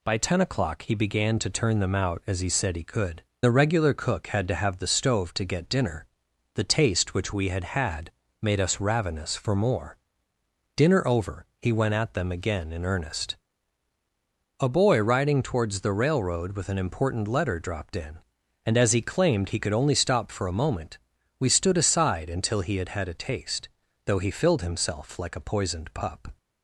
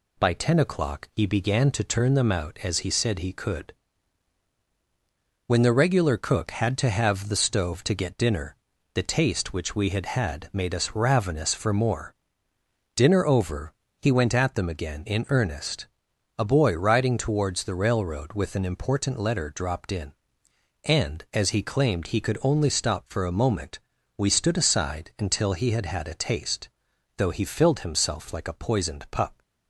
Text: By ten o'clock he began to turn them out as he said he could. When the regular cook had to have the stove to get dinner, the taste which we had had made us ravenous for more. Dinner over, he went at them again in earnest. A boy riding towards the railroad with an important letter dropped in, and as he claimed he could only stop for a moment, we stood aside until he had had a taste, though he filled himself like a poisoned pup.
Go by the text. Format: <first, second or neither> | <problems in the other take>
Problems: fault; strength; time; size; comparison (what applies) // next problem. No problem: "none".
second | skips "When"; at 3.3 s // pauses between "had" and "made"; slight; at 8.1 s; 0.32 s long